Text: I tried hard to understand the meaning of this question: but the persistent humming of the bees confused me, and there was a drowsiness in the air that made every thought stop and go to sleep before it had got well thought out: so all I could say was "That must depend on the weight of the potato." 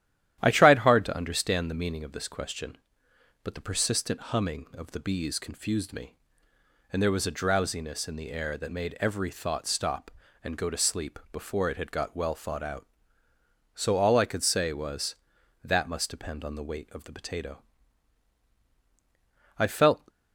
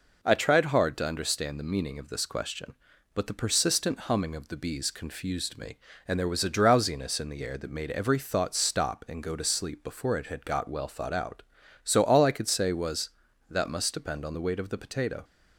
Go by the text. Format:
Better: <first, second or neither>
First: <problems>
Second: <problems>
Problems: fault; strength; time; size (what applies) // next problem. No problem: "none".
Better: second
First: starts louder than the rest; strong; until 1.4 s; 11.5 dB // goes on to say "I felt"; from 19.5 s on; 0.50 s long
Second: none